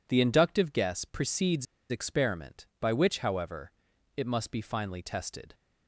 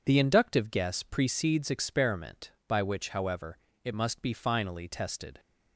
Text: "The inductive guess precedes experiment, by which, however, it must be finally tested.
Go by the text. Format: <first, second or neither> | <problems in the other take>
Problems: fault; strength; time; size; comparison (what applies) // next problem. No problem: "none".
second | pauses between "precedes" and "experiment"; slight; at 1.6 s; 0.24 s long